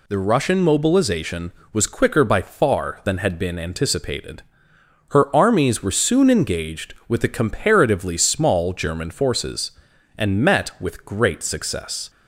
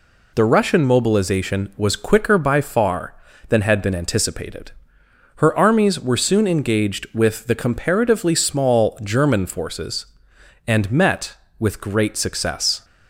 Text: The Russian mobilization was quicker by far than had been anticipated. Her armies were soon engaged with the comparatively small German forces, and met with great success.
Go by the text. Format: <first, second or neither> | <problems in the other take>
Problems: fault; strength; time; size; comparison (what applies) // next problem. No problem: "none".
neither | none